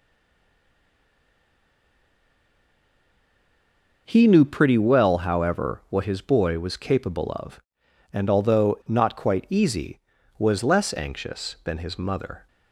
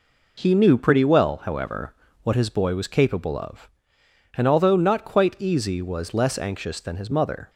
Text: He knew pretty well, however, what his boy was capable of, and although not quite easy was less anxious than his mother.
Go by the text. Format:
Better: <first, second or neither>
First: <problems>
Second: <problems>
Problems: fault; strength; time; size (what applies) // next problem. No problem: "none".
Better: second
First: stays silent before the first word; strong; until 4.0 s; 4.0 s long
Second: none